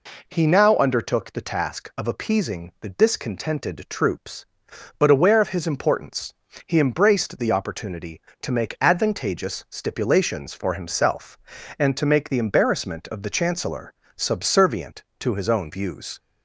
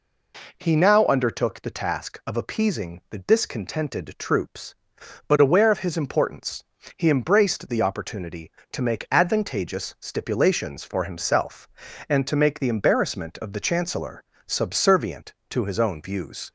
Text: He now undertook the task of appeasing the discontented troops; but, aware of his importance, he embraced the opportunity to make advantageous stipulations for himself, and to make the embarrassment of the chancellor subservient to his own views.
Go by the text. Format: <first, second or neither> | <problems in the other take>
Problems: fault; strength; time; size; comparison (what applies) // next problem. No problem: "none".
neither | pauses between "chancellor" and "subservient"; slight; the same in both